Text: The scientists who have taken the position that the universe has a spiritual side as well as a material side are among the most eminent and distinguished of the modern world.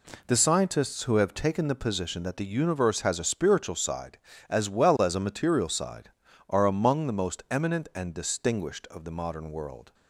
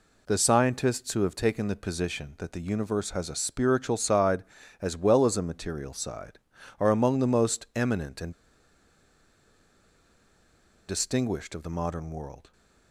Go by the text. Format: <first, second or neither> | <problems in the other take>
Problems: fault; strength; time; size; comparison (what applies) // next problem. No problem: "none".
first | pauses between "and" and "distinguished"; strong; at 8.3 s; 2.5 s long